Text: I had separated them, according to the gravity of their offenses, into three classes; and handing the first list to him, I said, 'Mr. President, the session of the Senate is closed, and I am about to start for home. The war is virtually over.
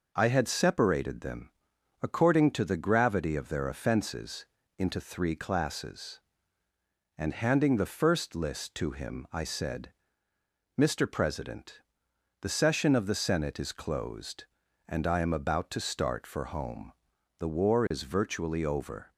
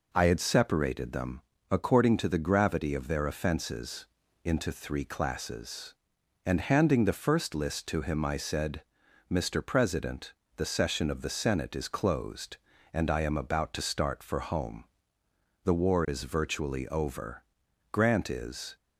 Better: first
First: none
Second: goes on to say "Grant is"; noticeable; from 17.8 s on; 0.86 s long

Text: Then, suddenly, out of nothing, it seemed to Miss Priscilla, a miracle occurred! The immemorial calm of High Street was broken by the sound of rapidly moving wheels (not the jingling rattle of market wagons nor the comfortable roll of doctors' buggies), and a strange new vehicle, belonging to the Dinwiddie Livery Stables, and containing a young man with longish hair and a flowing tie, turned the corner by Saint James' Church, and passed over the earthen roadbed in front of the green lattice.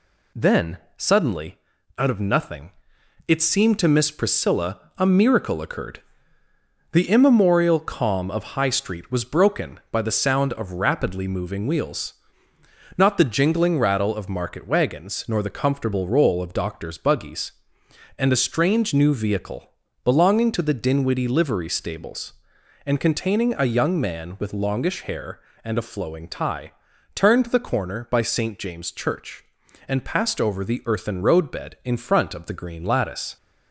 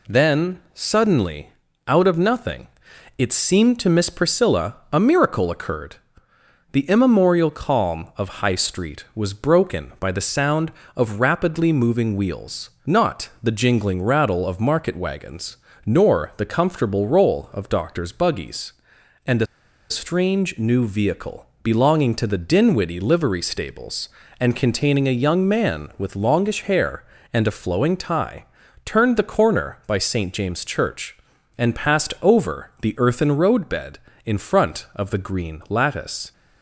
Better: first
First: none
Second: pauses between "wagons" and "nor"; slight; at 15.5 s; 0.30 s long // pauses between "a" and "strange"; at 19.4 s; 0.44 s long

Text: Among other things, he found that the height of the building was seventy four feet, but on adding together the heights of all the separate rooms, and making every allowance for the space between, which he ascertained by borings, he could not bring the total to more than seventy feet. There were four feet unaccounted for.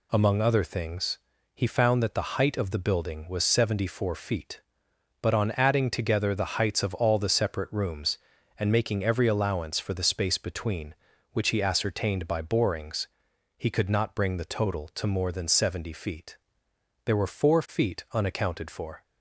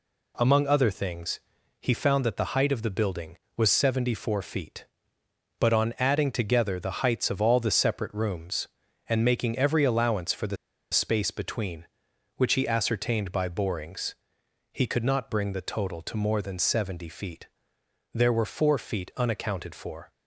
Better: first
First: none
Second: pauses between "the" and "space"; at 10.5 s; 0.36 s long

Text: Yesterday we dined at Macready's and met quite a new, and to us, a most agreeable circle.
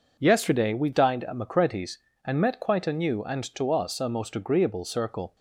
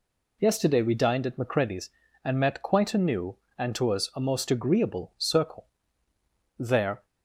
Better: first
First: none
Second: goes on to say "There"; slight; from 6.5 s on; 0.46 s long

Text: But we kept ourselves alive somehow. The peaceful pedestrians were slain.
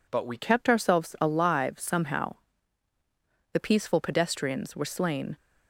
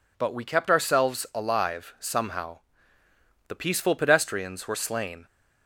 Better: second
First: changes voice at "kept"; from 0.3 s on; 5.0 s long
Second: none

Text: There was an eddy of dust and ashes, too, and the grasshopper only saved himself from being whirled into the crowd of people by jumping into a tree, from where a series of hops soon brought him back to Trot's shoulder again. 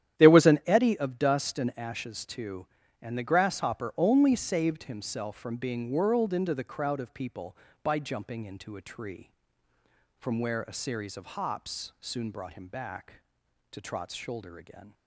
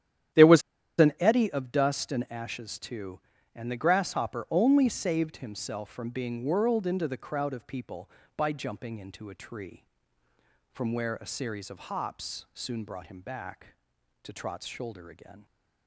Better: first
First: starts louder than the rest; strong; until 1.2 s; 10.5 dB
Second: starts louder than the rest; strong; until 1.7 s; 10.5 dB // pauses between "was" and "an"; at 0.6 s; 0.37 s long

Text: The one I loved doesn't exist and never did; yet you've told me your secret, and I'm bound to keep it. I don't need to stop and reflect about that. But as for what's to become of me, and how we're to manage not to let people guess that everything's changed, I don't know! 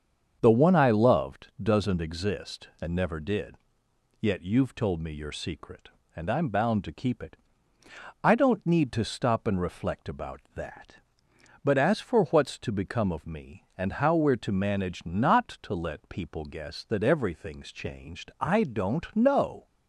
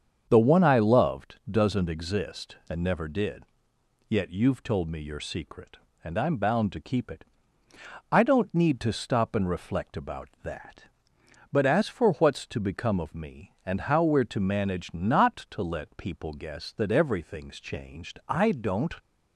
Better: first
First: starts louder than the rest; strong; until 1.4 s; 7.5 dB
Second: starts louder than the rest; strong; until 1.3 s; 7.5 dB // stops before "know"; at 19.0 s

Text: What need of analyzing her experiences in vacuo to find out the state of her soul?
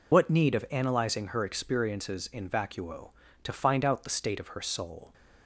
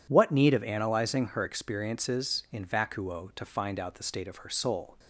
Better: second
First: loses the start of "What"; at 0.1 s; 65 ms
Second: none

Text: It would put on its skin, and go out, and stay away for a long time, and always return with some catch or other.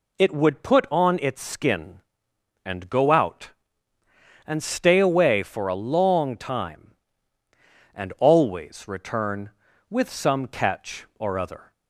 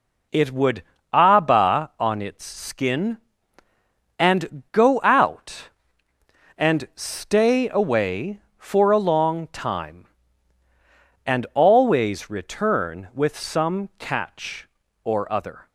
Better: first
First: none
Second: says "abba" for "put"; at 1.1 s

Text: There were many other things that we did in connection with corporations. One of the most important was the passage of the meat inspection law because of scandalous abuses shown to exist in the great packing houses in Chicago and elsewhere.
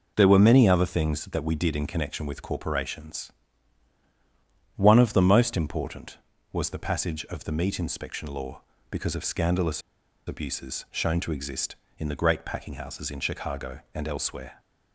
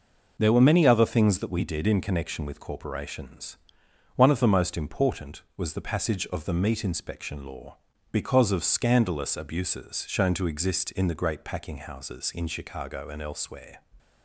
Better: second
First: pauses between "scandalous" and "abuses"; noticeable; at 9.8 s; 0.46 s long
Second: none

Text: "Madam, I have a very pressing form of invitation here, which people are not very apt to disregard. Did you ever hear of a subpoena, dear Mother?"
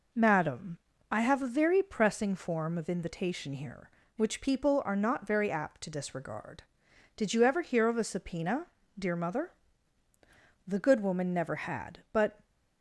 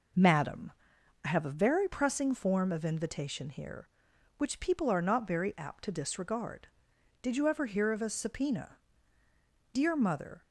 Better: second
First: goes on to say "The good woman never had but"; strong; from 10.6 s on; 1.7 s long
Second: none

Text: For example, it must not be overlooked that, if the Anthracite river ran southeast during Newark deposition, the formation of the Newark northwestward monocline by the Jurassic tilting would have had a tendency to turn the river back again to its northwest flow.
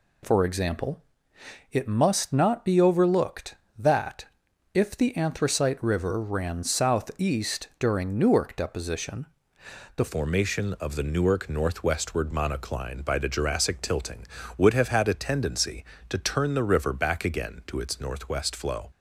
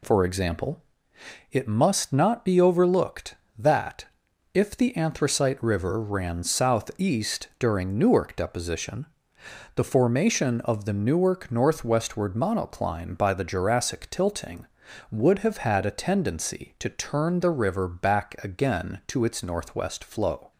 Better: second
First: changes voice at "formation"; from 10.0 s on; 8.8 s long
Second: none

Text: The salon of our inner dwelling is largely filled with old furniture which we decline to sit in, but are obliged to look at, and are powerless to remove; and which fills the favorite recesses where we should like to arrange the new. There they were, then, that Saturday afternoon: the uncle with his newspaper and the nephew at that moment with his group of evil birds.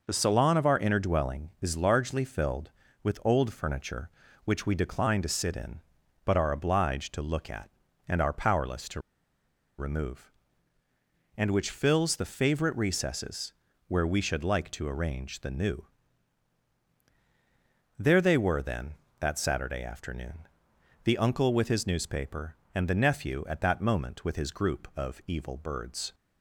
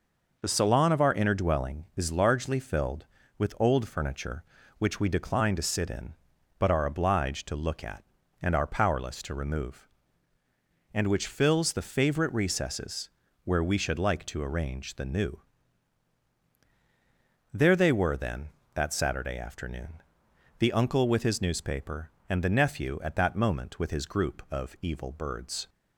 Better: second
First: pauses between "to" and "remove"; noticeable; at 8.9 s; 0.79 s long // pauses between "recesses" and "where"; slight; at 13.5 s; 0.36 s long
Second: pauses between "recesses" and "where"; slight; at 13.0 s; 0.36 s long

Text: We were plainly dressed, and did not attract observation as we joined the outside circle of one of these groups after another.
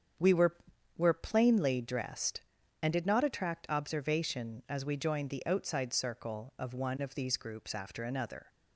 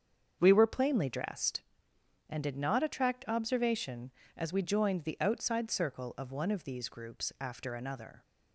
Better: second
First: starts louder than the rest; strong; until 1.5 s; 7.5 dB // says "were" twice; at 0.9 s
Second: starts louder than the rest; strong; until 1.4 s; 7 dB

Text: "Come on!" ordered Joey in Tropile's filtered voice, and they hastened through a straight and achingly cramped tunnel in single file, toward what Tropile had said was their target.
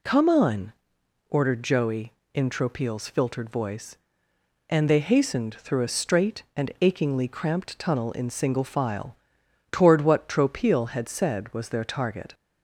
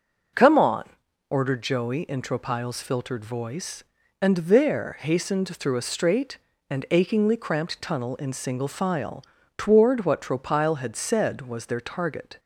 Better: first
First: none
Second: says "there" for "they"; at 4.3 s

